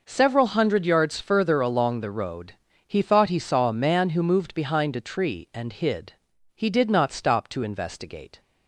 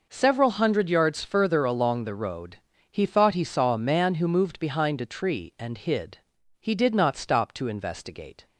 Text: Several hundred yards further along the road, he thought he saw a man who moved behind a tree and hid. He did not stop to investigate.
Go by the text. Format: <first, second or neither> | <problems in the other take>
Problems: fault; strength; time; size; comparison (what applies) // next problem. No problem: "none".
neither | none